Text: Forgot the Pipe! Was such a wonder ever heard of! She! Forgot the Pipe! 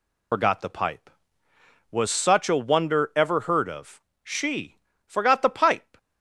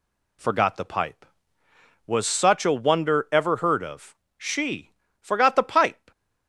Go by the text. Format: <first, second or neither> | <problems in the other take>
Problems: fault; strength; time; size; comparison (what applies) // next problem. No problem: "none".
second | loses the start of "Forgot"; at 0.3 s; 75 ms